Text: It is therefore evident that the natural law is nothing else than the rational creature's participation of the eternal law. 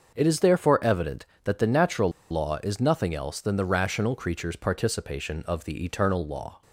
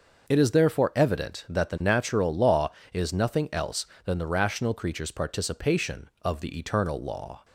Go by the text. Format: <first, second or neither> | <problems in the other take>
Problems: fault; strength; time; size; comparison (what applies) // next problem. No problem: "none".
second | starts louder than the rest; until 1.1 s; 6.5 dB // pauses between "natural" and "law"; slight; at 2.1 s; 0.19 s long